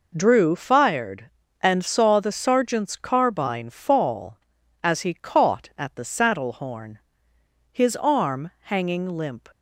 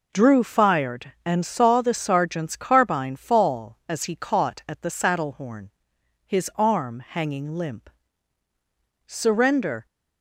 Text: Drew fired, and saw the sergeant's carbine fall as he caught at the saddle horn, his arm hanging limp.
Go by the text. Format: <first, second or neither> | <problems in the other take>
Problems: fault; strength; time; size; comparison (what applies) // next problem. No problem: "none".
first | goes on to say "Surrender"; noticeable; from 9.0 s on; 0.80 s long